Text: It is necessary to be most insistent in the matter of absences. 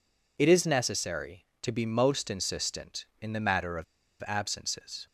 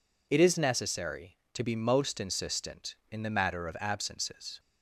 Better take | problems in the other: second | pauses between "of" and "absences"; at 3.8 s; 0.41 s long

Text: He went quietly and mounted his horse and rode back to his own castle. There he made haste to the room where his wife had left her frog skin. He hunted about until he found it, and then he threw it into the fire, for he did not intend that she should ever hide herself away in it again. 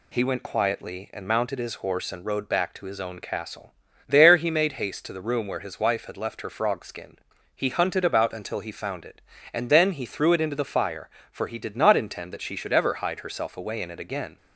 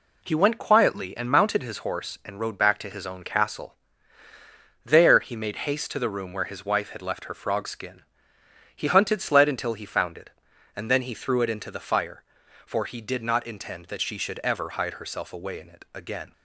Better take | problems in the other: first | says "sled" for "about"; at 9.2 s

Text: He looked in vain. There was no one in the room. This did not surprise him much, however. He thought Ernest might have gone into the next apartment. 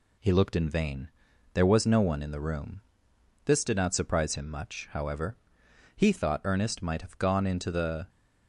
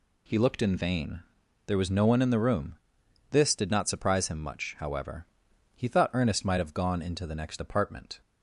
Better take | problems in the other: second | stops before "next apartment"; at 8.0 s

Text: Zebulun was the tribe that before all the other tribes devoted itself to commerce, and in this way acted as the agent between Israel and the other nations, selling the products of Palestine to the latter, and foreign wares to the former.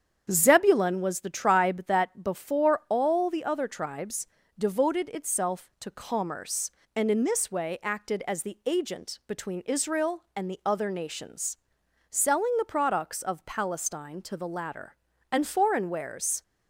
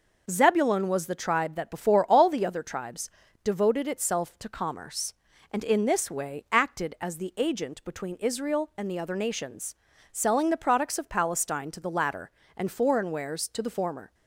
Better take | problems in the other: second | starts louder than the rest; strong; until 1.3 s; 8 dB // pauses between "tribes" and "devoted"; slight; at 4.2 s; 0.32 s long; slight in the second // stops before "to the former"; at 16.4 s

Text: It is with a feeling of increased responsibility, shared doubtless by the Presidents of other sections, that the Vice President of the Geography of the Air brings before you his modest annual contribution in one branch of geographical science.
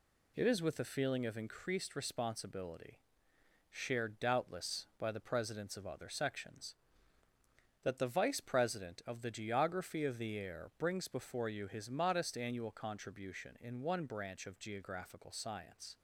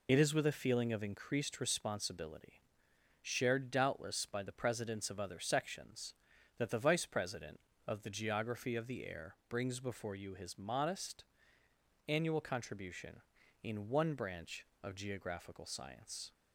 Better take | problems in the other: first | loses the start of "It"; at 0.0 s; 40 ms // pauses between "modest" and "annual"; noticeable; at 11.2 s; 0.82 s long

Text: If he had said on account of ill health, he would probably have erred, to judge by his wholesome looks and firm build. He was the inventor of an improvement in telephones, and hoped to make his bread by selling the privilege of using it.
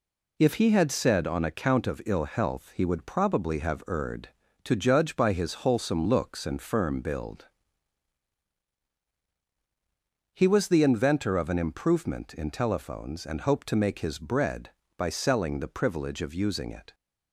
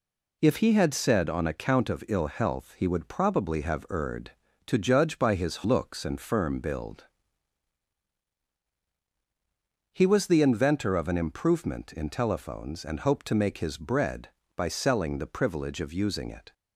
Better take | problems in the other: first | skips "wholesome"; at 5.6 s

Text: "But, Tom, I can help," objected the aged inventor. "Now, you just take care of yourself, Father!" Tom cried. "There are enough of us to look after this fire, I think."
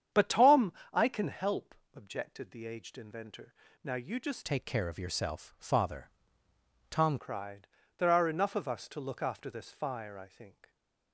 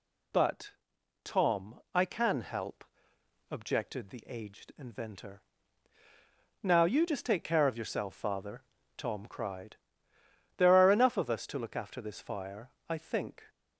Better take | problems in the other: second | starts louder than the rest; strong; until 1.3 s; 8.5 dB // changes voice from "take" to "Tom"; from 4.4 to 7.1 s; 2.7 s long

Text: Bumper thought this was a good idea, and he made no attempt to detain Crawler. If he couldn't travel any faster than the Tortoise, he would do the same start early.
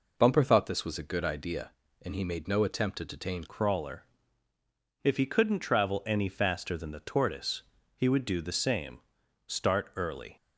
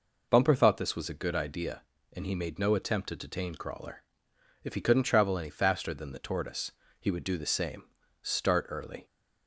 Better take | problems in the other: second | changes voice at "Crawler"; from 3.4 s on; 6.9 s long // pauses between "same" and "start"; noticeable; at 8.9 s; 0.46 s long; also in the second

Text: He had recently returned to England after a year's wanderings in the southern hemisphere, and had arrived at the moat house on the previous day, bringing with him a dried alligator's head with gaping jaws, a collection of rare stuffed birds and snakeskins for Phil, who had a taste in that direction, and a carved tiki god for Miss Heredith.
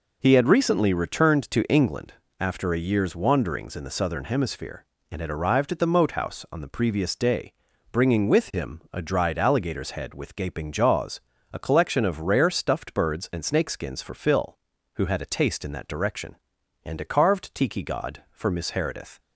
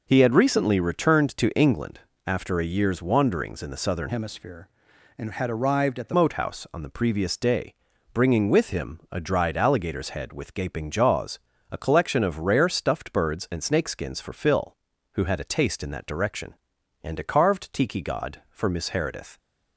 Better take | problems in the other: first | pauses between "England" and "after"; slight; at 1.9 s; 0.26 s long; slight in the first // changes voice from "hemisphere" to "the"; from 4.0 to 6.1 s; 2.1 s long

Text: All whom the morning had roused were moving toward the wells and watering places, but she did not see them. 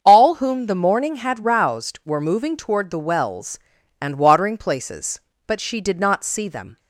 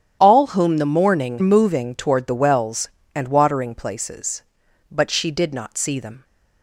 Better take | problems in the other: first | starts louder than the rest; strong; until 1.2 s; 10 dB; also in the first // skips "had roused were"; at 1.3 s

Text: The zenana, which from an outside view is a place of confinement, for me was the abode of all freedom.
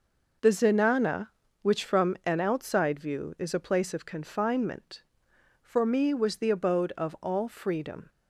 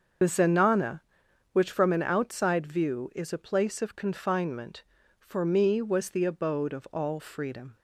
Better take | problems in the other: first | loses the start of "The"; at 0.2 s; 55 ms // starts louder than the rest; until 1.7 s; 6.5 dB

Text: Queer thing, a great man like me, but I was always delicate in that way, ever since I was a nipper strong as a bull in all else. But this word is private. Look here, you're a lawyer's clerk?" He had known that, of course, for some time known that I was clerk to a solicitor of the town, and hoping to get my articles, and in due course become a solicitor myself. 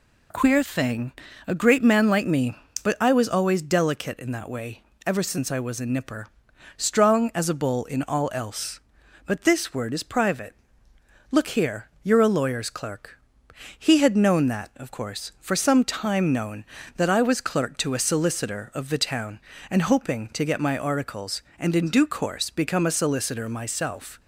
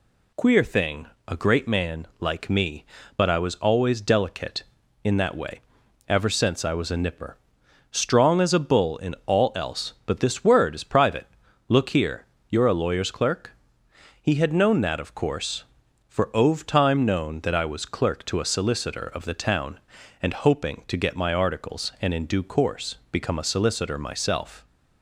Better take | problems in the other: first | pauses between "nipper" and "strong"; noticeable; at 7.3 s; 0.58 s long; noticeable in the first // says "ove" for "some"; at 16.3 s

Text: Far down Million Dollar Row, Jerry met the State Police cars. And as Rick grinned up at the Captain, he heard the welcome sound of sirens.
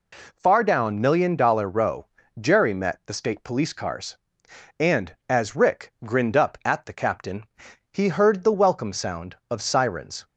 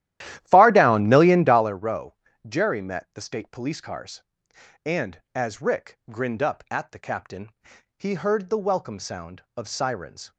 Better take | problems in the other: first | starts louder than the rest; strong; until 1.8 s; 13 dB

